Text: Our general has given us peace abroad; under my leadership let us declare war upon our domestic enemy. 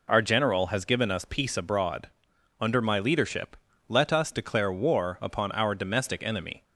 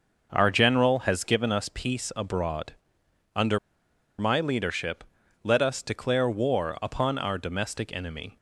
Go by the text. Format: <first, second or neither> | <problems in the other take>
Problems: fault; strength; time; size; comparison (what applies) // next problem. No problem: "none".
first | pauses between "under" and "my"; noticeable; at 3.5 s; 0.59 s long // pauses between "leadership" and "let"; at 5.0 s; 0.40 s long; slight in the first